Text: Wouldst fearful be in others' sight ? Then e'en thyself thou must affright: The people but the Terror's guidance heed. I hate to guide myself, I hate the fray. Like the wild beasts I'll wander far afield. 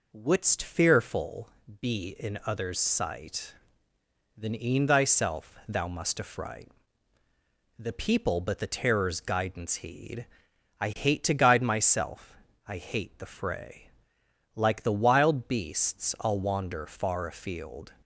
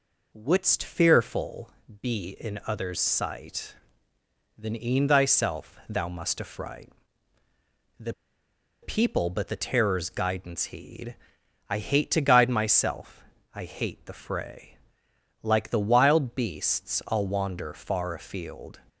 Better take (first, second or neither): first